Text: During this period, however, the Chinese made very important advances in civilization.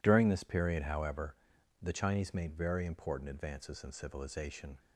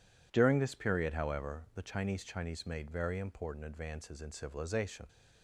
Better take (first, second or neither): first